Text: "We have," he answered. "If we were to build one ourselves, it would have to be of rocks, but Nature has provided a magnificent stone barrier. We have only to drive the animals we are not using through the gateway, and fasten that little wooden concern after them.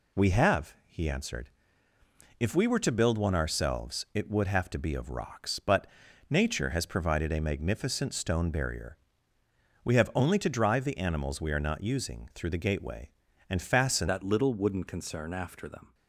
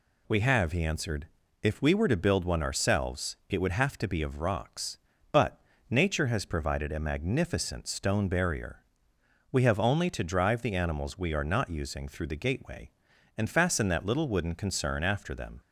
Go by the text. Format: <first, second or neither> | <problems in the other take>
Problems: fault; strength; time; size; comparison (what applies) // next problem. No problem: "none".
second | pauses between "but" and "Nature"; at 5.8 s; 0.42 s long; slight in the second // changes voice at "that"; from 14.0 s on; 1.9 s long